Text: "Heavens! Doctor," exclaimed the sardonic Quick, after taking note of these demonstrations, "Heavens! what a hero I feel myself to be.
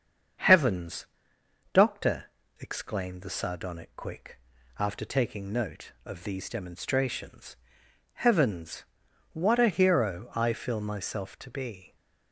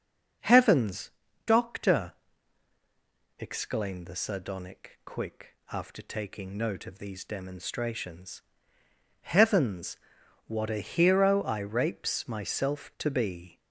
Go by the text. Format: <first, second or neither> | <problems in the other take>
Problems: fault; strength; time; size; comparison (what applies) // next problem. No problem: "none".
first | starts louder than the rest; until 1.7 s; 6.5 dB; strong in the first // says "rapes" for "feel"; at 11.5 s